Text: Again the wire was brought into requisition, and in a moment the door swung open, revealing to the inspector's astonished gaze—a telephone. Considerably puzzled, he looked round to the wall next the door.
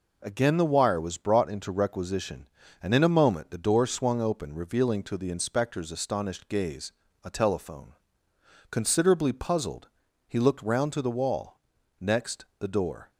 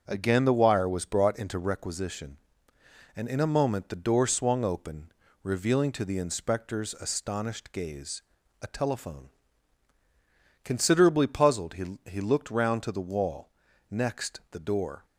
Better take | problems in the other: first | starts louder than the rest; until 1.0 s; 6.5 dB // says "he" twice; at 12.0 s // pauses between "wall" and "next"; at 13.4 s; 0.40 s long; also in the first

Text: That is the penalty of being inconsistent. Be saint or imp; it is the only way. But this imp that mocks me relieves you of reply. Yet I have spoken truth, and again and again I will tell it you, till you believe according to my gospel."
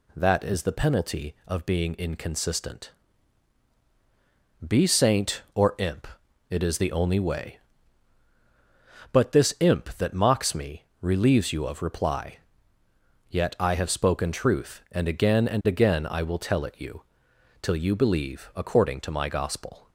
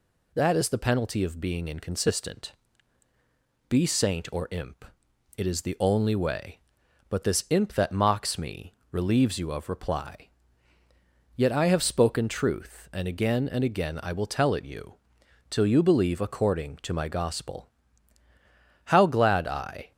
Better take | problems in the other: first | pauses between "me" and "relieves"; slight; at 8.7 s; 0.18 s long; slight in the first // goes on to say "How glad I"; noticeable; from 18.8 s on; 1.0 s long

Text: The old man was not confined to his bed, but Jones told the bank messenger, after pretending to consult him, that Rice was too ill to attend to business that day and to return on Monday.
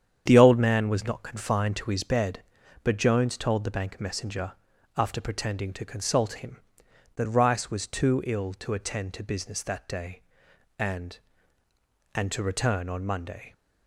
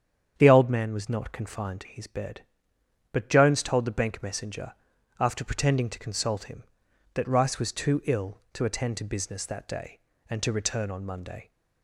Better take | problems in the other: second | starts louder than the rest; strong; until 1.2 s; 8.5 dB; strong in the second // says "and" twice; at 12.1 s

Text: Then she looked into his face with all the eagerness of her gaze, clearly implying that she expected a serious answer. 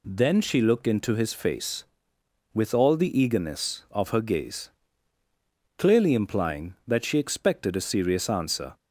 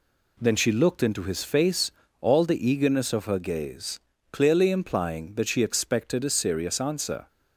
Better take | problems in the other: first | skips "with"; at 2.0 s

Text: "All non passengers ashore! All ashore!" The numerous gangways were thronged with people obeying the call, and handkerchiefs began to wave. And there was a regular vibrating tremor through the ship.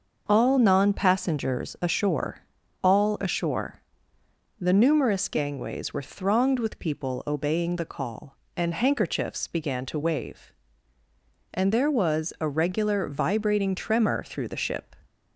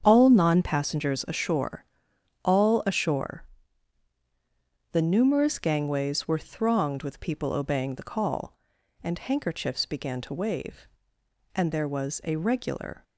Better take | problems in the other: first | starts louder than the rest; strong; until 1.0 s; 8 dB; also in the first // stops before "vibrating tremor through the ship"; at 13.0 s

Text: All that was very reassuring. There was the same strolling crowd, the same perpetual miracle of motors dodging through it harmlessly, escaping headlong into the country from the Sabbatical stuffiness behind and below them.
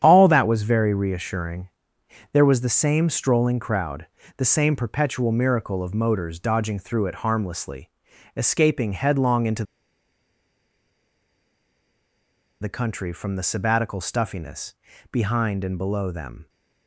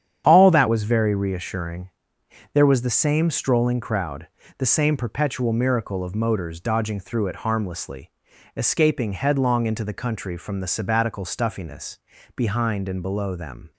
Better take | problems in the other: second | starts louder than the rest; strong; until 1.0 s; 9 dB; strong in the second // pauses between "into" and "the"; strong; at 9.6 s; 2.9 s long // pauses between "stuffiness" and "behind"; at 14.7 s; 0.38 s long; also in the second

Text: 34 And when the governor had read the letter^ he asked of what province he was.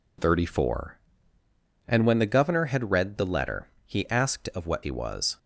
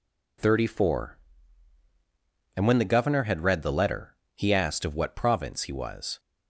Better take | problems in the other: second | pauses between "letter" and "he"; slight; at 3.6 s; 0.18 s long; slight in the second // skips "province"; at 4.8 s

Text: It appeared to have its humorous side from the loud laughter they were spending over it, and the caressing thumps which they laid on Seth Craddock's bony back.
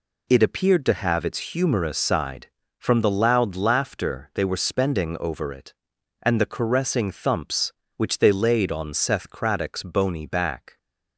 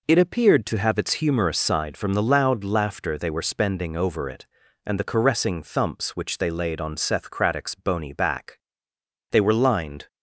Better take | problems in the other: first | goes on to say "They were lined"; noticeable; from 9.3 s on; 0.76 s long

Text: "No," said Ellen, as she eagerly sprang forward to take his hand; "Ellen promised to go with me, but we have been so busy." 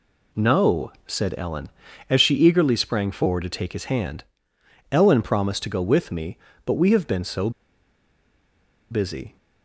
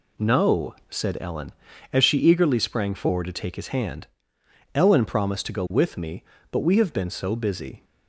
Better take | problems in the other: second | pauses between "so" and "busy"; strong; at 7.4 s; 1.4 s long

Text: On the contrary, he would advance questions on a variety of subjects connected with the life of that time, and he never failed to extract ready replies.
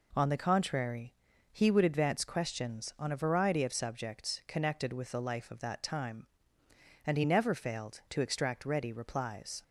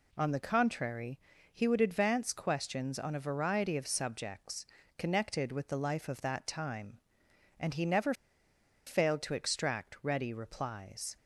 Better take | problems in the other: first | pauses between "subjects" and "connected"; slight; at 4.6 s; 0.32 s long // pauses between "never" and "failed"; noticeable; at 8.1 s; 0.73 s long

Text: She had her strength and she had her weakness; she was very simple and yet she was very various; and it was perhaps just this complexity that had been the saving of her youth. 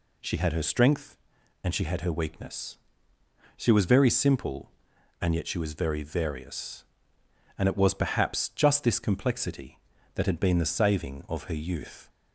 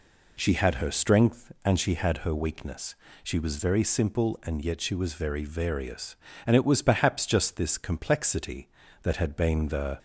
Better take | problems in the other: first | stops before "saving of her youth"; at 9.9 s

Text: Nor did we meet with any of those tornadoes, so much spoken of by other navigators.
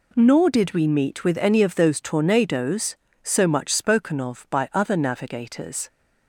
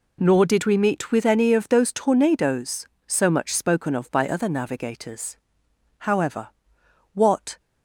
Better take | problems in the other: first | goes on to say "However what"; from 5.9 s on; 1.6 s long

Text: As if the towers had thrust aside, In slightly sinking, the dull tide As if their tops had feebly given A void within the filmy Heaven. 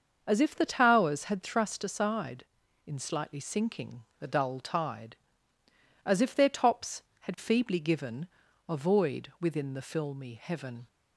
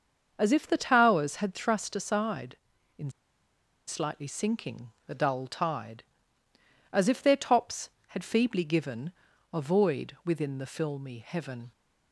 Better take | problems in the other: first | starts louder than the rest; until 1.3 s; 6.5 dB; also in the first // pauses between "In" and "slightly"; noticeable; at 3.1 s; 0.75 s long // pauses between "given" and "A"; at 9.1 s; 0.40 s long; also in the first

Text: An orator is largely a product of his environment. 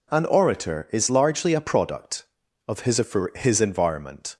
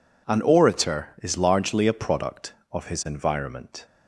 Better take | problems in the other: second | says "his" twice; at 3.3 s

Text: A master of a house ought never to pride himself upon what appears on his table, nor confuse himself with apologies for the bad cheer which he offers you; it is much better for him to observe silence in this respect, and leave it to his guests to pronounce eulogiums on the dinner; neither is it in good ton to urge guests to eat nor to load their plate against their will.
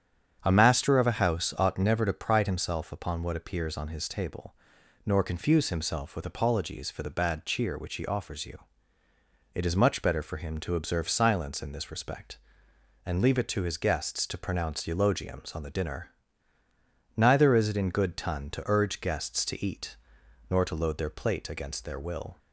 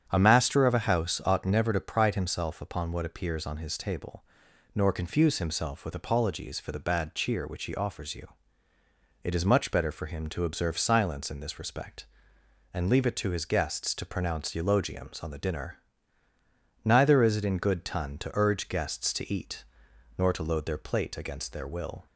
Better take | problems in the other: neither | starts louder than the rest; strong; the same in both // pauses between "eat" and "nor"; noticeable; the same in both

